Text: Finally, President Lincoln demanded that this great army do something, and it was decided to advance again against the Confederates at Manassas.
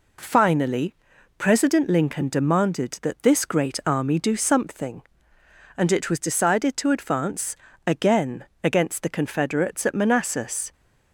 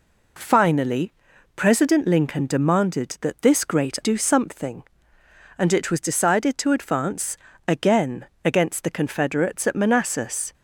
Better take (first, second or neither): first